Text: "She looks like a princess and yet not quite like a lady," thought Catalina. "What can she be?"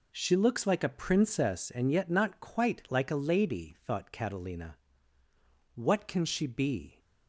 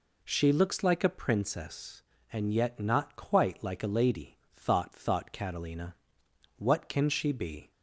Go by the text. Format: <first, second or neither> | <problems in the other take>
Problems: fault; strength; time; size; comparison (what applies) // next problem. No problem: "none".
first | says "thought" twice; at 4.9 s